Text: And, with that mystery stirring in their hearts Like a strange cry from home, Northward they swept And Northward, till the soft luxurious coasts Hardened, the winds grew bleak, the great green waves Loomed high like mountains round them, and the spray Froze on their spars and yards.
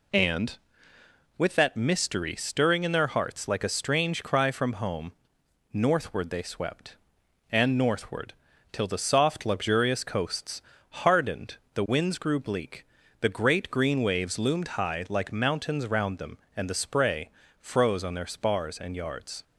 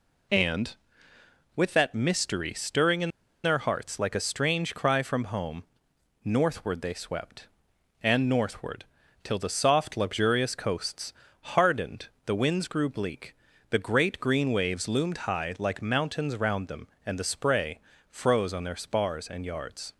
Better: first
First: pauses between "coasts" and "Hardened"; slight; at 10.6 s; 0.28 s long // pauses between "spray" and "Froze"; slight; at 17.2 s; 0.32 s long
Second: pauses between "in" and "their"; slight; at 3.0 s; 0.34 s long // pauses between "coasts" and "Hardened"; slight; at 11.1 s; 0.28 s long // pauses between "spray" and "Froze"; slight; at 17.7 s; 0.32 s long

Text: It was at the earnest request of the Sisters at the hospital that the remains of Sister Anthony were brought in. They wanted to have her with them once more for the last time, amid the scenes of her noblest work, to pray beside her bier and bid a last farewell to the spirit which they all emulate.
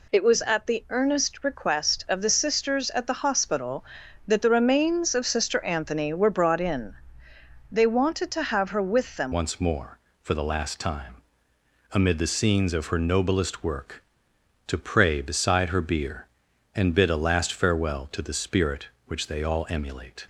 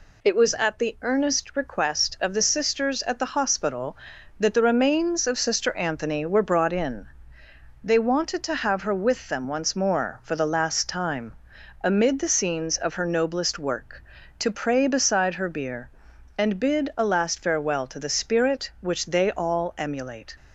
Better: second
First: changes voice at "once"; from 9.3 s on; 10.9 s long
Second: none

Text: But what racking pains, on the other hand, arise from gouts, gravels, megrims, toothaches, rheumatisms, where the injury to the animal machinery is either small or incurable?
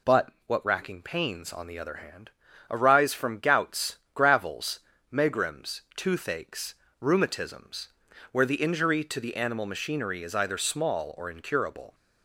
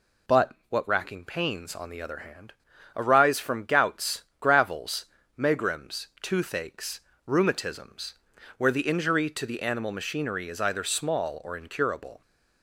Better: neither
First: pauses between "But" and "what"; slight; at 0.3 s; 0.16 s long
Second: pauses between "But" and "what"; slight; at 0.5 s; 0.16 s long

